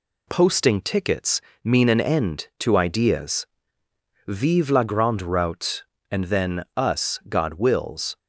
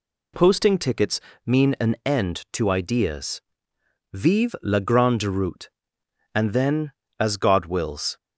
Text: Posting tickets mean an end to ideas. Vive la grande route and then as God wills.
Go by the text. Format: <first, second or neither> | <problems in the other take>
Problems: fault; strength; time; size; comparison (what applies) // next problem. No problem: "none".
second | pauses between "tickets" and "mean"; slight; at 1.3 s; 0.24 s long; slight in the second // says "us" for "as"; at 6.7 s